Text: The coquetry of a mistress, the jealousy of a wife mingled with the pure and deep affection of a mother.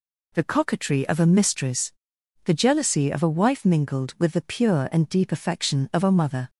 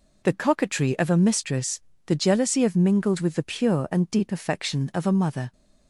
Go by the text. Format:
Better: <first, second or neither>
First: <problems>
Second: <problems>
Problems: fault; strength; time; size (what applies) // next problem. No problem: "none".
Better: first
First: none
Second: skips "a wife"; at 2.7 s